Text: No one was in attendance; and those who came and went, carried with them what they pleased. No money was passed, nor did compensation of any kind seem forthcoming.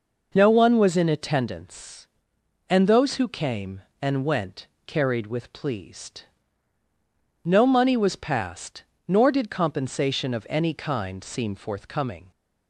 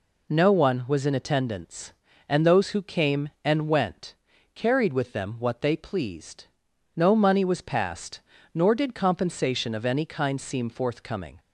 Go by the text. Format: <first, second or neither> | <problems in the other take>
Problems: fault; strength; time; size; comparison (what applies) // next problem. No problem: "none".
second | skips "them what they"; at 5.5 s